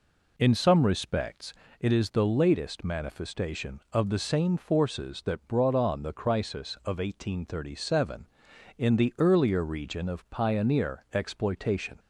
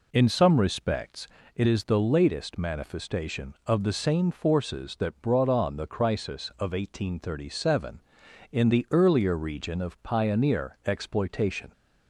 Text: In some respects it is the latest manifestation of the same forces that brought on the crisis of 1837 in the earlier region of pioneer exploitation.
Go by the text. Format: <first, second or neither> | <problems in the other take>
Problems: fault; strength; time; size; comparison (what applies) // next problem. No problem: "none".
neither | pauses between "respects" and "it"; slight; the same in both